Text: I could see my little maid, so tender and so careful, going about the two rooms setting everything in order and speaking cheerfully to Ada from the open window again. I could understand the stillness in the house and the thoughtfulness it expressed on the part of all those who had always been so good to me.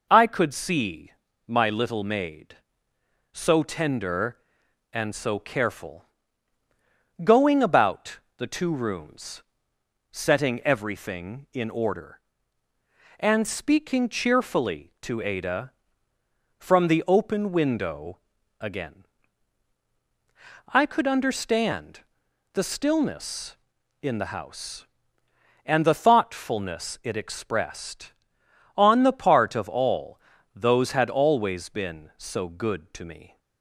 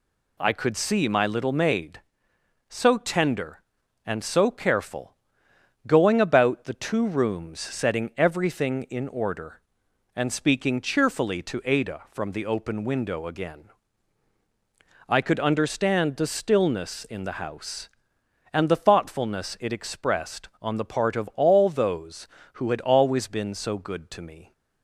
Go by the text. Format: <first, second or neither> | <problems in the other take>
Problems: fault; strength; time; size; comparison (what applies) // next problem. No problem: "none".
second | pauses between "see" and "my"; slight; at 1.1 s; 0.34 s long // pauses between "about" and "the"; slight; at 8.1 s; 0.20 s long // pauses between "rooms" and "setting"; noticeable; at 9.4 s; 0.68 s long // pauses between "window" and "again"; noticeable; at 18.1 s; 0.46 s long // pauses between "understand" and "the"; noticeable; at 22.0 s; 0.54 s long // pauses between "all" and "those"; slight; at 30.2 s; 0.34 s long // skips "who"; at 30.9 s